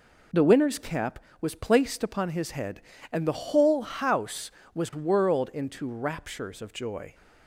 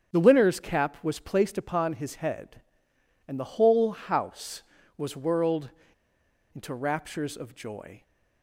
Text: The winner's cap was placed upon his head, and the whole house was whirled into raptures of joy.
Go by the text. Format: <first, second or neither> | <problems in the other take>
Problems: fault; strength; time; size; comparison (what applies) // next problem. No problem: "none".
first | starts louder than the rest; strong; until 1.1 s; 8 dB // pauses between "whirled" and "into"; noticeable; at 5.7 s; 0.83 s long